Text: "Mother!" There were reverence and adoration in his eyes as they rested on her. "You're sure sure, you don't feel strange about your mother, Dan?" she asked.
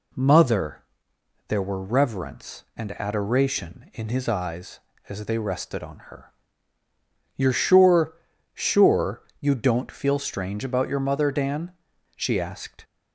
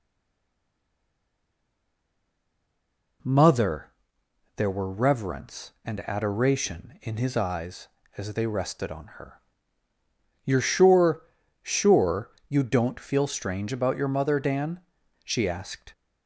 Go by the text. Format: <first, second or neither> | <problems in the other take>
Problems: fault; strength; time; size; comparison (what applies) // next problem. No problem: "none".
first | stays silent before the first word; strong; until 3.2 s; 3.2 s long // pauses between "sure" and "sure"; at 11.1 s; 0.42 s long; also in the first